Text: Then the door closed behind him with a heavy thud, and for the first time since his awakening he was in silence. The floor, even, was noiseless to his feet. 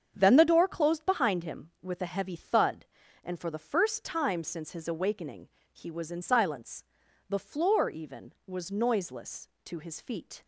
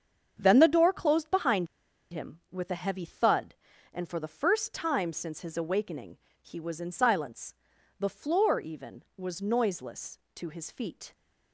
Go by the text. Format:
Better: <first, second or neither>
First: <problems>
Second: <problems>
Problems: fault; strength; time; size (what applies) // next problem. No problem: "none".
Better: first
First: starts louder than the rest; strong; until 1.1 s; 7.5 dB // pauses between "awakening" and "he"; slight; at 5.4 s; 0.24 s long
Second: starts louder than the rest; strong; until 1.3 s; 7.5 dB // pauses between "behind" and "him"; at 1.6 s; 0.45 s long // pauses between "awakening" and "he"; slight; at 6.1 s; 0.24 s long